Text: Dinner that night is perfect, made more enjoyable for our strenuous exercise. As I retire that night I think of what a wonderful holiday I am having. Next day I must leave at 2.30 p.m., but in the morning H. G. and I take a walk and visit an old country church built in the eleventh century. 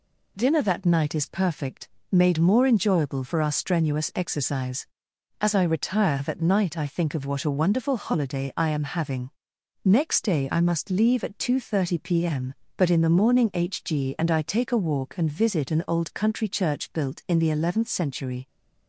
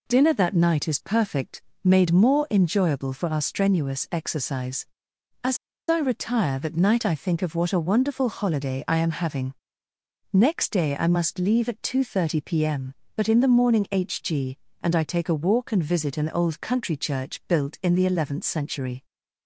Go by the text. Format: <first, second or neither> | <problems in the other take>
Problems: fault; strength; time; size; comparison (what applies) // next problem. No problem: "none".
first | pauses between "As" and "I"; slight; at 5.5 s; 0.31 s long